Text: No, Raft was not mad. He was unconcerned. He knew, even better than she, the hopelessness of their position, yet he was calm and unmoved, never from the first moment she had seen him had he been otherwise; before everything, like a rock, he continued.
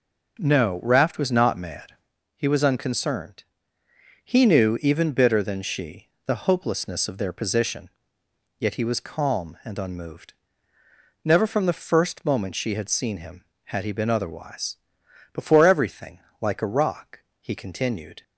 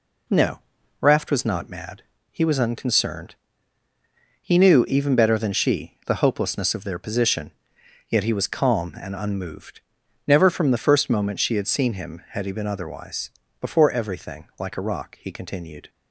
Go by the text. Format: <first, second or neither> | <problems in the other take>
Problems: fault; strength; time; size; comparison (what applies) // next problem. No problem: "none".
second | says "bitter" for "better"; at 5.1 s